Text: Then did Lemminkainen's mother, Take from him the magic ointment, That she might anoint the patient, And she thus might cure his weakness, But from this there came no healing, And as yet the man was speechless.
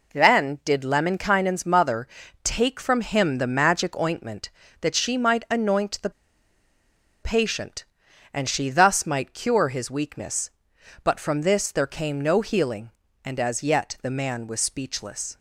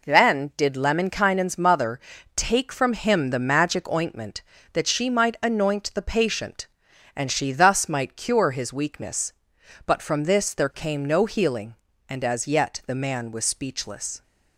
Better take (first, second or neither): second